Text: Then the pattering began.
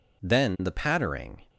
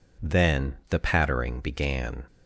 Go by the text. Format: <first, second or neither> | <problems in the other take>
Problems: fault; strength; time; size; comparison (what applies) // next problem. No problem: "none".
second | stops before "began"; at 1.4 s